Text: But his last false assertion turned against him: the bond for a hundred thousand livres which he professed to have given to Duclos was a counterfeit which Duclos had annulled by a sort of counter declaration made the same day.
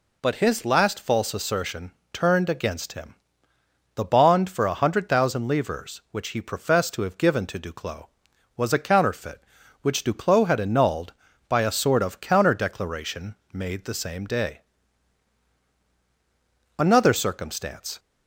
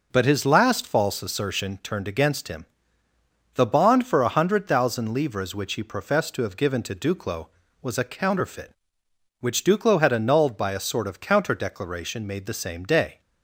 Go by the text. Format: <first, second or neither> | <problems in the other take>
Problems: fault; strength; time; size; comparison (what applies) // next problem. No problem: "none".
second | pauses between "assertion" and "turned"; slight; at 1.9 s; 0.20 s long // pauses between "declaration" and "made"; slight; at 13.3 s; 0.18 s long // goes on to say "Another circumstance"; noticeable; from 16.7 s on; 1.2 s long